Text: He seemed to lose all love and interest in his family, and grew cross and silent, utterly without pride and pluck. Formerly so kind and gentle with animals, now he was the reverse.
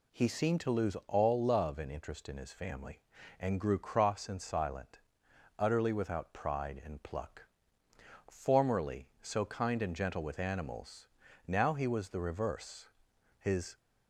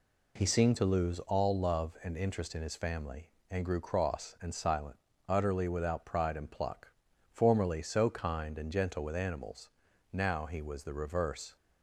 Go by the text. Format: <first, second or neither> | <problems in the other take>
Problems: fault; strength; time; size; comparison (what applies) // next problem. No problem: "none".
second | goes on to say "His"; slight; from 13.3 s on; 0.38 s long